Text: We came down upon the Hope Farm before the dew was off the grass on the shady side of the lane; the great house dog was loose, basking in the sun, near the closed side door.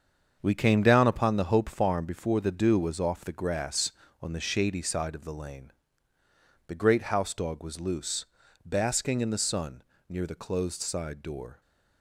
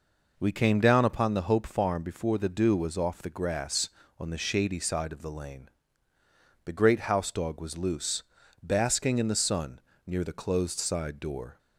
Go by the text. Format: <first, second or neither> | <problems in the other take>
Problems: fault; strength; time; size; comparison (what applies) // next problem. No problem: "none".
second | gets quieter; strong; throughout; 7.5 dB